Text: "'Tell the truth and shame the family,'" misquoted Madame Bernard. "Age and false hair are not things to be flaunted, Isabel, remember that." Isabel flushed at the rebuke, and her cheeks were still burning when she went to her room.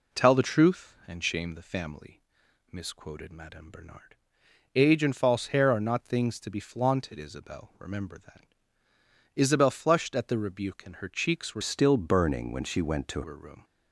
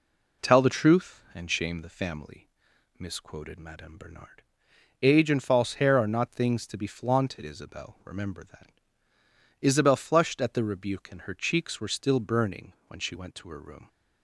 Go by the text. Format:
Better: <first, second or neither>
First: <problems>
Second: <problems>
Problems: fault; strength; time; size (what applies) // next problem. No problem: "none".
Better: second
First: changes voice from "still" to "to"; from 11.6 to 13.2 s; 1.6 s long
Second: none